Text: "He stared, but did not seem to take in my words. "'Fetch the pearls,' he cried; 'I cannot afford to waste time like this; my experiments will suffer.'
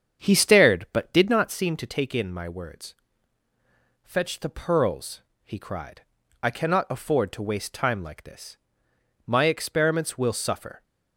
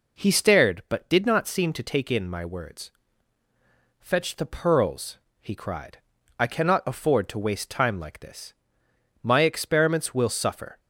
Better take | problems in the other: second | starts louder than the rest; strong; until 1.5 s; 7.5 dB

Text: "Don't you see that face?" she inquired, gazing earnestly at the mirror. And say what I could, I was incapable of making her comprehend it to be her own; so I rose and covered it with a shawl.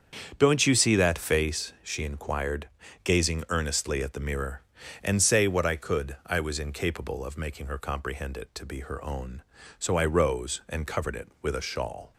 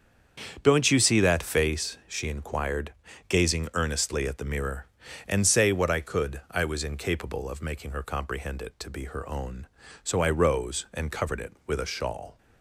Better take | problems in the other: neither | starts louder than the rest; strong; the same in both

